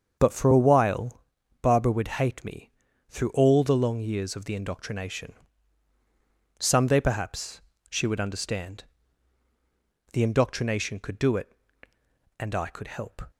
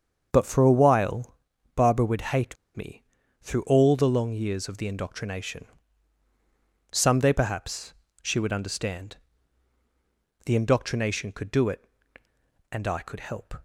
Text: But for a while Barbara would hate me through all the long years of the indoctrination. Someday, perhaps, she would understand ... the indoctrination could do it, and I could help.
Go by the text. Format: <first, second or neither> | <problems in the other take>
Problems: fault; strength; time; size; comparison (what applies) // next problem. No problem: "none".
first | starts louder than the rest; until 1.3 s; 7 dB; also in the first // pauses between "while" and "Barbara"; at 1.3 s; 0.38 s long; also in the first // pauses between "hate" and "me"; slight; at 2.5 s; 0.20 s long // pauses between "me" and "through"; at 3.0 s; 0.40 s long; also in the first